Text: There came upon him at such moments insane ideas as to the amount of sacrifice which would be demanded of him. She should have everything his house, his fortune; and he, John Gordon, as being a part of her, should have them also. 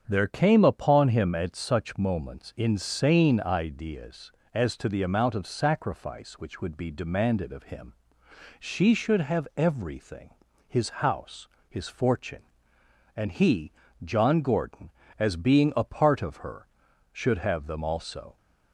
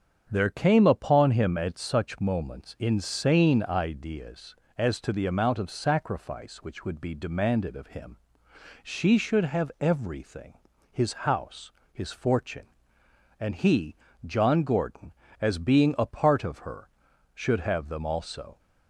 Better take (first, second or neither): neither